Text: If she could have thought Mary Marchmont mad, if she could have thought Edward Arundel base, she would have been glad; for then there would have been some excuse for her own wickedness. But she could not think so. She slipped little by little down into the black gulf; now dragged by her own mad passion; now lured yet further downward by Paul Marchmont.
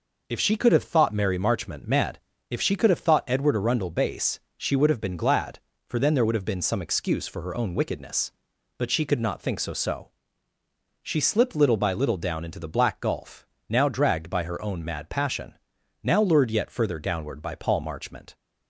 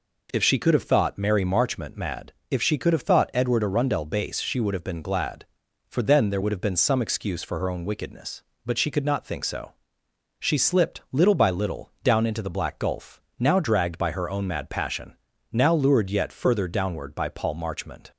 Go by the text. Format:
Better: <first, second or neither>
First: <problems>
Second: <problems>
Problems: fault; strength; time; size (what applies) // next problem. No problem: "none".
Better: second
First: says "so" twice; at 9.7 s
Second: none